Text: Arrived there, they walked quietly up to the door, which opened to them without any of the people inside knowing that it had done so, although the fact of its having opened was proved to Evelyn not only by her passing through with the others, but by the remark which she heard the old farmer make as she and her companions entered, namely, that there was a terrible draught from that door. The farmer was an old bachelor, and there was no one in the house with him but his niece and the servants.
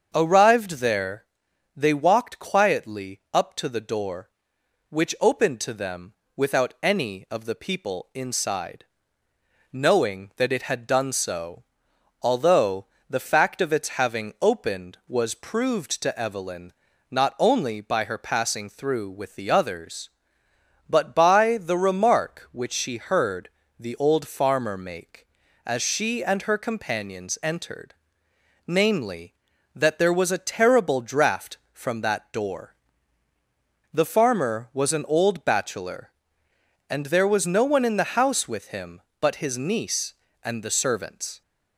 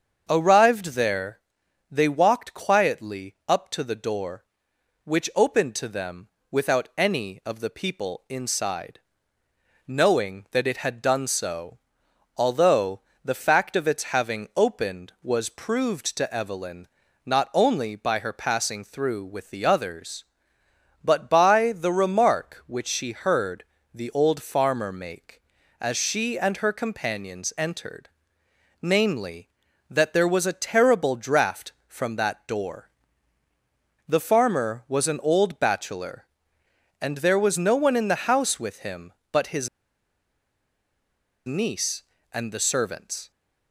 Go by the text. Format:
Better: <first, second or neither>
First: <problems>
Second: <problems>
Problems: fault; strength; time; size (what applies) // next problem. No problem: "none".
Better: first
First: starts louder than the rest; until 1.1 s; 7 dB // pauses between "them" and "without"; slight; at 6.1 s; 0.24 s long // pauses between "inside" and "knowing"; noticeable; at 8.8 s; 0.90 s long // pauses between "although" and "the"; slight; at 12.8 s; 0.24 s long // pauses between "Evelyn" and "not"; slight; at 16.7 s; 0.36 s long // pauses between "heard" and "the"; slight; at 23.4 s; 0.32 s long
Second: starts louder than the rest; until 1.2 s; 7 dB // pauses between "them" and "without"; slight; at 6.2 s; 0.24 s long // pauses between "inside" and "knowing"; noticeable; at 8.9 s; 0.90 s long // pauses between "although" and "the"; slight; at 12.9 s; 0.24 s long // pauses between "Evelyn" and "not"; slight; at 16.8 s; 0.36 s long // pauses between "heard" and "the"; slight; at 23.6 s; 0.32 s long // pauses between "his" and "niece"; strong; at 39.6 s; 1.7 s long